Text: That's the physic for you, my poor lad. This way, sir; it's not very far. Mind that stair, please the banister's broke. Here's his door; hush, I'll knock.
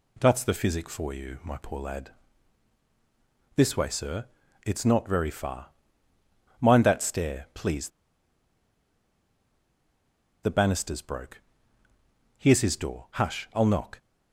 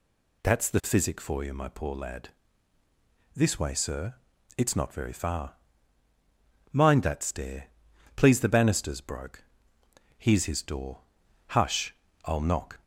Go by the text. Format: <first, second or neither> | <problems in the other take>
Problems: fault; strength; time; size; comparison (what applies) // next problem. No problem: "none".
second | pauses between "please" and "the"; strong; at 7.8 s; 2.5 s long